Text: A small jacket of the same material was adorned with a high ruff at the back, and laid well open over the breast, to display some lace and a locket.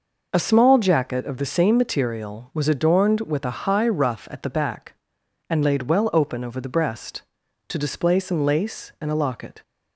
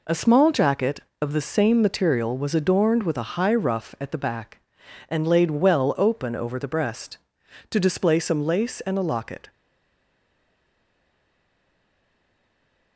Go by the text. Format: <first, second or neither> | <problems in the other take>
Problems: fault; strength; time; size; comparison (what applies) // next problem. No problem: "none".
first | stays silent after the last word; strong; from 9.4 s on; 3.5 s long